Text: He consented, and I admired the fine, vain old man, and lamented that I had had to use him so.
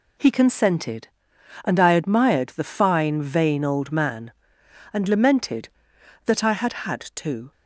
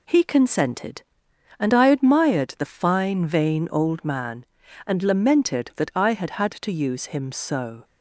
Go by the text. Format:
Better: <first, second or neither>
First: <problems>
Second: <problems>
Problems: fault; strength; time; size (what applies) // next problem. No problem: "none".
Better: second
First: stops before "use him so"; at 7.5 s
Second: none